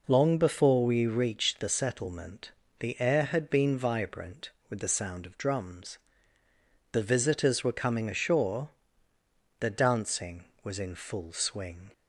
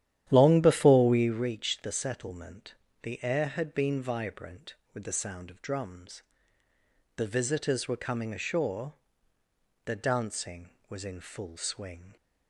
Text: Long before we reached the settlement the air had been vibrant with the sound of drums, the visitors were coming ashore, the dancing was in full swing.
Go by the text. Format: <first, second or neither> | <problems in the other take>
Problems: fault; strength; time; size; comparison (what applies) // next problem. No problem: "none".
first | starts louder than the rest; strong; until 1.4 s; 11 dB // pauses between "settlement" and "the"; slight; at 2.7 s; 0.28 s long; slight in the first